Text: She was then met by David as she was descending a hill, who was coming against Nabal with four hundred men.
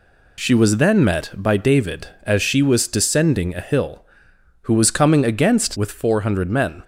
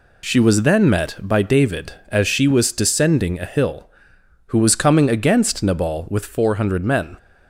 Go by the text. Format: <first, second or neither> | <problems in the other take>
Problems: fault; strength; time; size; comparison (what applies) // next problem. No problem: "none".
second | skips "Nabal"; at 5.7 s